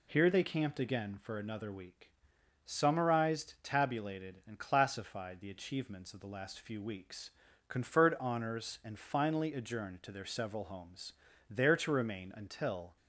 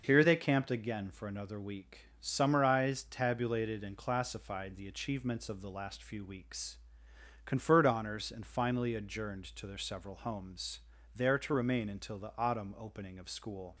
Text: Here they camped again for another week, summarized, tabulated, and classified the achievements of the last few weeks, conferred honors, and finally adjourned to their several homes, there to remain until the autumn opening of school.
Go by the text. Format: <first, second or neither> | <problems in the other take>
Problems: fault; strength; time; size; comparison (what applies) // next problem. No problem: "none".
second | stops before "the autumn opening of school"; at 12.9 s